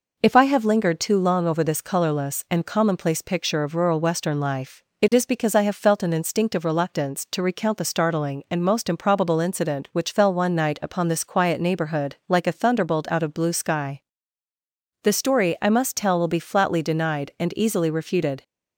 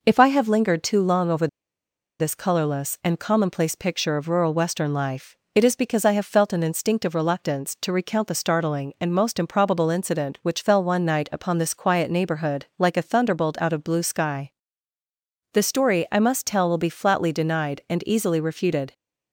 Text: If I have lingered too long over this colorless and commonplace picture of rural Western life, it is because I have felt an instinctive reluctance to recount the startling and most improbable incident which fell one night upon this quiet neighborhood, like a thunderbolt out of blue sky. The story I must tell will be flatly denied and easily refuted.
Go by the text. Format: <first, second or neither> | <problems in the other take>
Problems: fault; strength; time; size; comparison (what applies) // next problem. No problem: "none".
first | pauses between "over" and "this"; noticeable; at 1.4 s; 0.72 s long